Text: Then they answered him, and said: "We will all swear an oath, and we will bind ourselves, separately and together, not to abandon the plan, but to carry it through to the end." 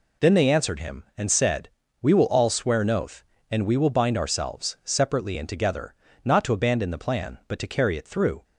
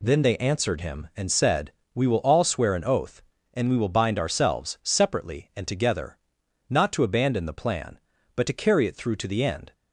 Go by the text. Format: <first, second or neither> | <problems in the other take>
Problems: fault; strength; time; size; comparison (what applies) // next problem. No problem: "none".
second | stops before "to the end"; at 8.4 s